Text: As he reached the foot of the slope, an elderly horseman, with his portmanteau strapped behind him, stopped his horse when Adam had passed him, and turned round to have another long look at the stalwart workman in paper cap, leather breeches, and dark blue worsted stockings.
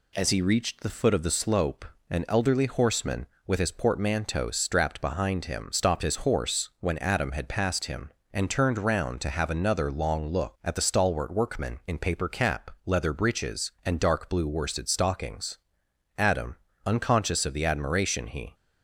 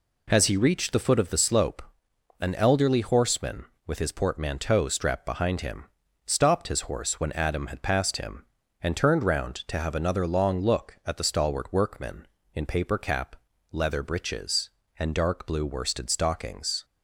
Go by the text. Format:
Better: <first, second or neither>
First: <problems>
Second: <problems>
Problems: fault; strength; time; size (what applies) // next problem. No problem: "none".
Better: second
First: goes on to say "Adam unconscious of the admiration he"; strong; from 16.1 s on; 2.3 s long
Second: none